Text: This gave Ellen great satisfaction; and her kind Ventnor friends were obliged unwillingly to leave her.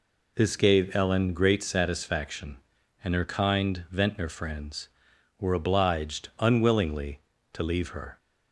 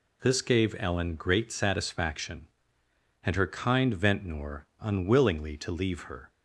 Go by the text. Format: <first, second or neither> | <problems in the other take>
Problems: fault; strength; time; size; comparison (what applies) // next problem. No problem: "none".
first | skips "friends were obliged"; at 4.7 s